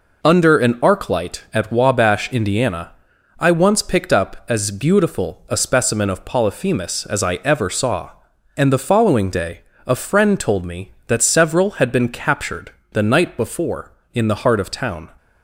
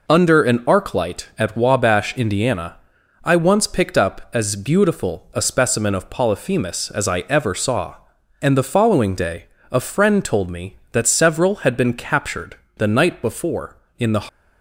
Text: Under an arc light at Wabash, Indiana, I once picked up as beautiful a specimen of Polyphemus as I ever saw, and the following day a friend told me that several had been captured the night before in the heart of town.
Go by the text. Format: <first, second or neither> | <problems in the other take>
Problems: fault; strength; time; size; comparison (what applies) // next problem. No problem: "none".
first | pauses between "day" and "a"; slight; at 9.4 s; 0.24 s long; slight in the first // pauses between "captured" and "the"; slight; at 12.5 s; 0.20 s long; slight in the first // stops before "heart of town"; at 14.2 s